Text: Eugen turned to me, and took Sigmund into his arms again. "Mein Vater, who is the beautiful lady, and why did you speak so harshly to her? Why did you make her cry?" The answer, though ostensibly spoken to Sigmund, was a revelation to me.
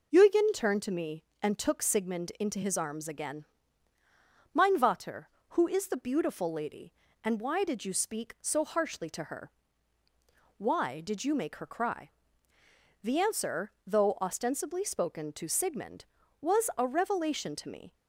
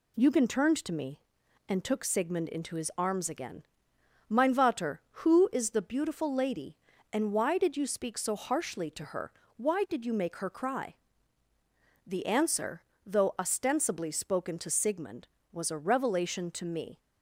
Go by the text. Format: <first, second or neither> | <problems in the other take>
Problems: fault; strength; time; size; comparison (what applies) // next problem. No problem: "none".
neither | none